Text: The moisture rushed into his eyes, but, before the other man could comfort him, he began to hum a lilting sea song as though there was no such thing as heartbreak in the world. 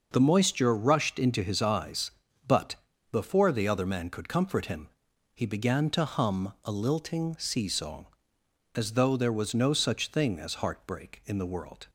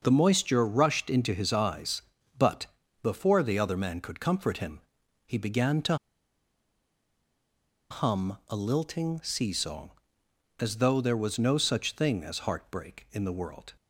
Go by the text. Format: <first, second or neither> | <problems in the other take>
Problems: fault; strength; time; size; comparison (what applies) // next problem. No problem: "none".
first | pauses between "to" and "hum"; strong; at 5.9 s; 1.9 s long